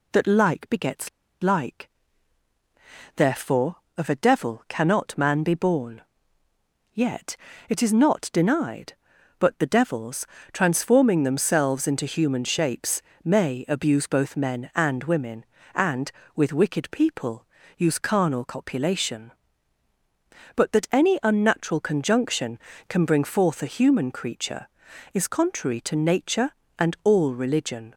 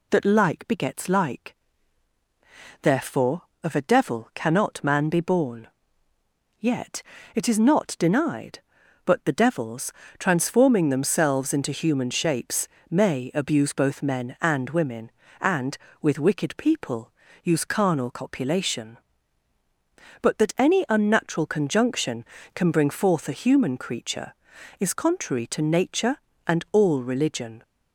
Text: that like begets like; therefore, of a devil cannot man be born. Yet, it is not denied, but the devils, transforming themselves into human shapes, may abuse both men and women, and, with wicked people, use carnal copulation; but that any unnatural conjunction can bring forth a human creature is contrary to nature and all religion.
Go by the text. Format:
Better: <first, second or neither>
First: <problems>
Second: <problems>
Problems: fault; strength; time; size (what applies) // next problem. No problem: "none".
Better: second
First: pauses between "begets" and "like"; slight; at 1.0 s; 0.32 s long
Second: none